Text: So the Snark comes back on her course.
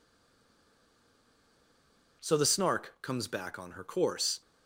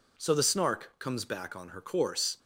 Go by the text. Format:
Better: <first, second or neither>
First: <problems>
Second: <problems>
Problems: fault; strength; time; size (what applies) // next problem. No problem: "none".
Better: second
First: stays silent before the first word; until 2.2 s; 2.2 s long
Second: none